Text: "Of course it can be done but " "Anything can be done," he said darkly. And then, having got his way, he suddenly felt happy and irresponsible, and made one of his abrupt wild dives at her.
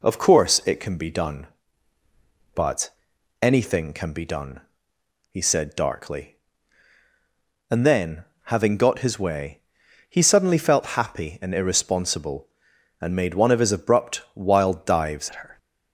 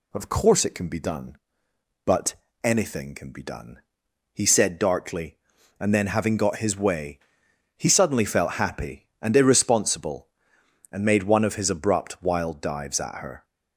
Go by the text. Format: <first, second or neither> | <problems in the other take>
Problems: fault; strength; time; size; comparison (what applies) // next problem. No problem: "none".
second | changes voice at "at"; from 15.2 s on; 0.3 s long